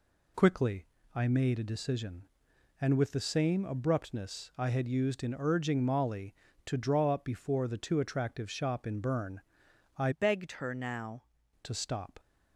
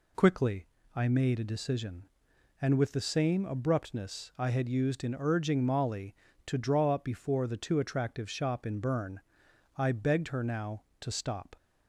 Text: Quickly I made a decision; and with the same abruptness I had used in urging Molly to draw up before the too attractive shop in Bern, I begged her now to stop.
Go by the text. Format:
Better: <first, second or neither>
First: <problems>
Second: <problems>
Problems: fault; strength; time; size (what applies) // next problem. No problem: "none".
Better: second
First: pauses between "Quickly" and "I"; slight; at 0.8 s; 0.28 s long // changes voice from "begged" to "now"; from 10.1 to 11.2 s; 1.1 s long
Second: pauses between "Quickly" and "I"; slight; at 0.6 s; 0.28 s long